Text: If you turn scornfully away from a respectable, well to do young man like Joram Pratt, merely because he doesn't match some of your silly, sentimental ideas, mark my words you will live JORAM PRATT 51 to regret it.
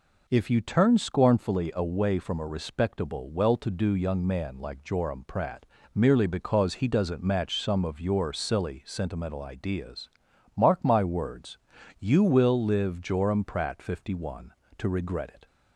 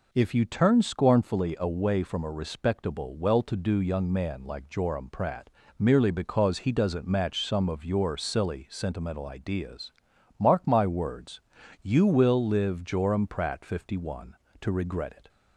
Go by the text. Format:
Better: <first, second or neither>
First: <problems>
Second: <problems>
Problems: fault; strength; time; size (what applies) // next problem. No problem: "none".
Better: neither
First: pauses between "words" and "you"; at 11.5 s; 0.42 s long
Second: pauses between "words" and "you"; at 11.4 s; 0.42 s long